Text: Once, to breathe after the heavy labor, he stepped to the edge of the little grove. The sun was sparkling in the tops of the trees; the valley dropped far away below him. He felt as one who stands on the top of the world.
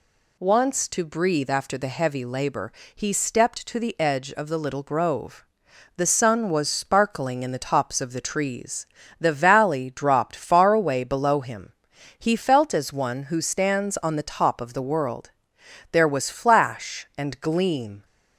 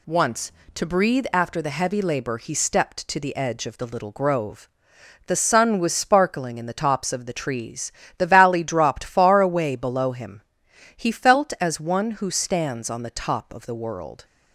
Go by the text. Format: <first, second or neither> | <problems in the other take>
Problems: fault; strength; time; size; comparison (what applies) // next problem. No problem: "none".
second | goes on to say "There was flash and gleam"; strong; from 15.9 s on; 2.1 s long